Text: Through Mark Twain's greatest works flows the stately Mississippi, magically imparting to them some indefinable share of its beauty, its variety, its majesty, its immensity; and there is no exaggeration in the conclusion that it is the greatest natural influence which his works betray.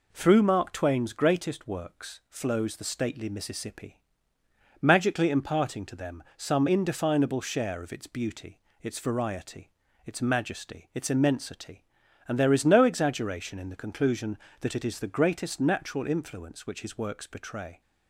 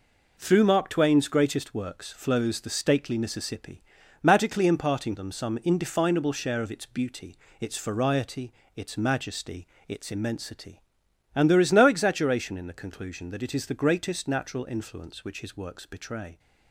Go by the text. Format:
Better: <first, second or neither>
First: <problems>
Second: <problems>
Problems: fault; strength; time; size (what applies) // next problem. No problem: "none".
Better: first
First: none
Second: skips "to"; at 5.1 s